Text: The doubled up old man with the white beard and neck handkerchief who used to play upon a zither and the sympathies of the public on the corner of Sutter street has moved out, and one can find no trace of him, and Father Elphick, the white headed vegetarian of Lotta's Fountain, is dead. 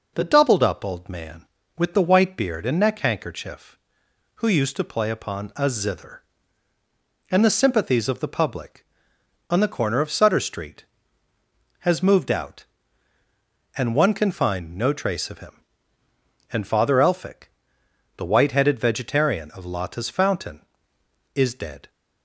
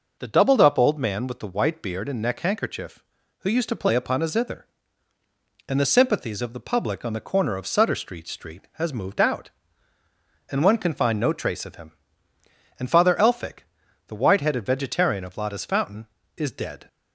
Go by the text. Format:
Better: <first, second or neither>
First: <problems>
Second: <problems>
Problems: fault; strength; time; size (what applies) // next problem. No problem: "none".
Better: first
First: none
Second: says "street" twice; at 8.2 s